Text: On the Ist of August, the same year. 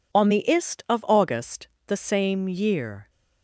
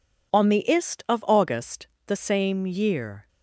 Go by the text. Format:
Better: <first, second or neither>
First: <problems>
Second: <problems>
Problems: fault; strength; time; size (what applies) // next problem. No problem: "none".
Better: neither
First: none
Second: none